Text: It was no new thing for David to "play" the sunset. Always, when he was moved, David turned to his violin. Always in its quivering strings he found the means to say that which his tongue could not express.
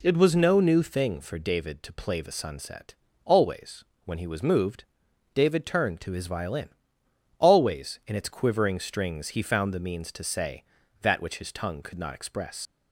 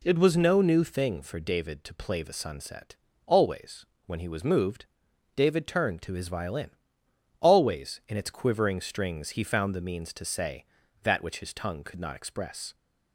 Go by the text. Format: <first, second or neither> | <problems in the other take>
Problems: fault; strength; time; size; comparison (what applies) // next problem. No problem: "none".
second | leaves "express" unfinished; at 12.6 s; 80 ms